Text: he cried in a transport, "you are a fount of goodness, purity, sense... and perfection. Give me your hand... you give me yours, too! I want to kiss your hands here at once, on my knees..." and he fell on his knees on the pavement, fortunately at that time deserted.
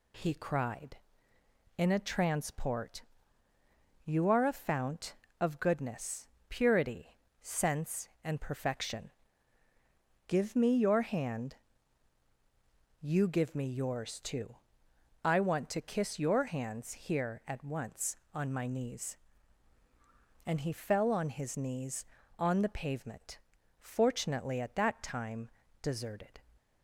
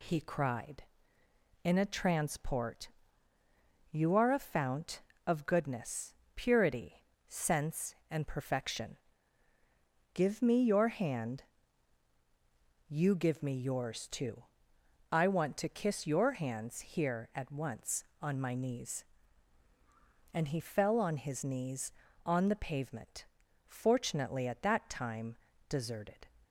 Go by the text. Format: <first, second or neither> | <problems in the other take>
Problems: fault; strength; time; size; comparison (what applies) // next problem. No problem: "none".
neither | pauses between "time" and "deserted"; slight; the same in both